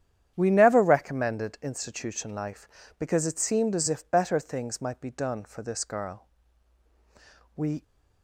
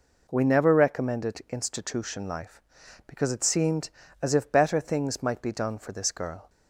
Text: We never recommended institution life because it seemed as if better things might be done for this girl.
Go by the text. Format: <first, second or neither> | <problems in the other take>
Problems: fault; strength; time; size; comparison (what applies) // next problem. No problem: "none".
second | starts louder than the rest; strong; until 1.3 s; 9.5 dB // goes on to say "We"; slight; from 7.5 s on; 0.28 s long